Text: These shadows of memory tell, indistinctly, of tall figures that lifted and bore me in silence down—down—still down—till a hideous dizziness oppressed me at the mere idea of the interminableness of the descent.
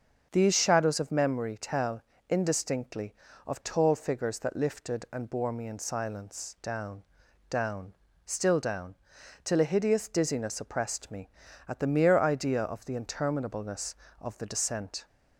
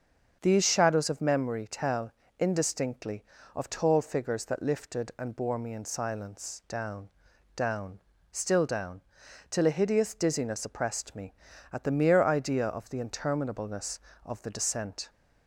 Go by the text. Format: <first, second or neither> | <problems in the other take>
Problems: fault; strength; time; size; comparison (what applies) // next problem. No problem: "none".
neither | starts louder than the rest; the same in both